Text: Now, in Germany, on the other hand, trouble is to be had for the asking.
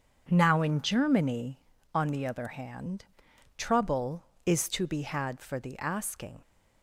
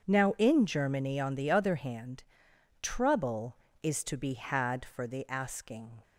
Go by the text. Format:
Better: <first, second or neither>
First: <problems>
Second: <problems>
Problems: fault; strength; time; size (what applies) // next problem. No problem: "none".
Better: neither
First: starts louder than the rest; strong; until 1.3 s; 7 dB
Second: starts louder than the rest; until 1.1 s; 7 dB